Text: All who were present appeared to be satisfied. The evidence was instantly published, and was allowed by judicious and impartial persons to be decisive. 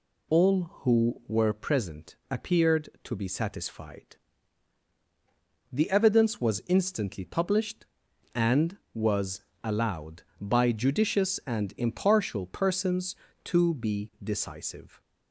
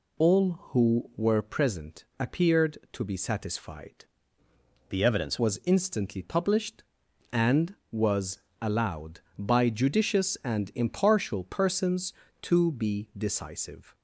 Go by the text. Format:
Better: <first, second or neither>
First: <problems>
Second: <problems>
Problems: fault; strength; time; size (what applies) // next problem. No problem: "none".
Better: first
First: pauses between "present" and "appeared"; slight; at 2.1 s; 0.16 s long // pauses between "was" and "allowed"; slight; at 9.4 s; 0.22 s long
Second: pauses between "present" and "appeared"; slight; at 2.0 s; 0.16 s long // changes voice from "The" to "evidence"; from 4.8 to 5.3 s; 0.5 s long // pauses between "was" and "allowed"; slight; at 8.3 s; 0.22 s long